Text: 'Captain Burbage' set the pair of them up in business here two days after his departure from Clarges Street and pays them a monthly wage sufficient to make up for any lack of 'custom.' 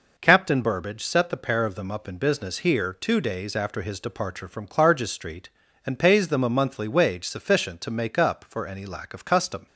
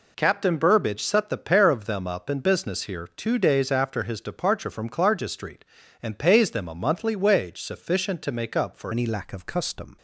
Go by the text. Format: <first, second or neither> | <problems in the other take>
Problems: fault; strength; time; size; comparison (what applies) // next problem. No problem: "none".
first | changes voice at "any"; from 8.9 s on; 1.0 s long